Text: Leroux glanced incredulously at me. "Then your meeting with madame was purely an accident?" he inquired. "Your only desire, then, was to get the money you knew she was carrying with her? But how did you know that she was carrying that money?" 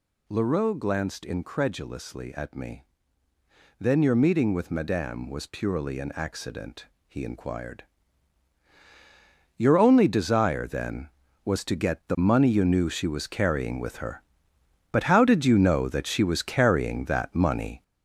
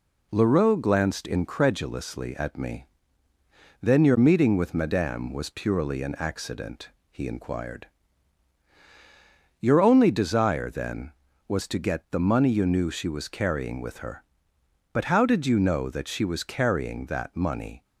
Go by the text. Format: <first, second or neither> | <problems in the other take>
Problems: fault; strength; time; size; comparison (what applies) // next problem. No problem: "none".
second | gets louder; noticeable; throughout; 6 dB